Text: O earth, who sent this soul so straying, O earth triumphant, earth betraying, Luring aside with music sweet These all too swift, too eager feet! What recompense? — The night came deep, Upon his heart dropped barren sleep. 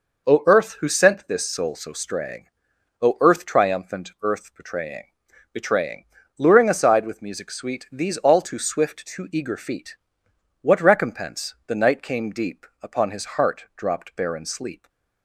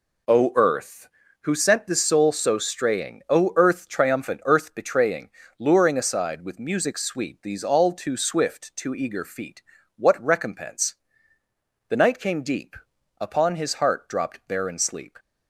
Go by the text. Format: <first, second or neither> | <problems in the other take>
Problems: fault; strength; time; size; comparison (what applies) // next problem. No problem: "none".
second | says "betraying" twice; at 5.5 s